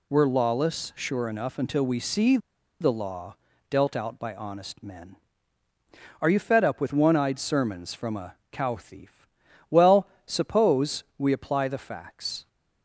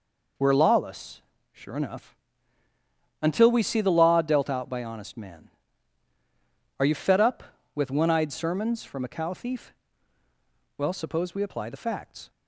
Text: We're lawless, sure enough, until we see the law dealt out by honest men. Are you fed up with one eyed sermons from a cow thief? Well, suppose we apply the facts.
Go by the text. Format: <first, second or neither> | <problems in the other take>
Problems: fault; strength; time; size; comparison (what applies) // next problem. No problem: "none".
second | pauses between "see" and "the"; at 2.3 s; 0.43 s long // pauses between "law" and "dealt"; slight; at 3.3 s; 0.34 s long // pauses between "a" and "cow"; slight; at 8.3 s; 0.18 s long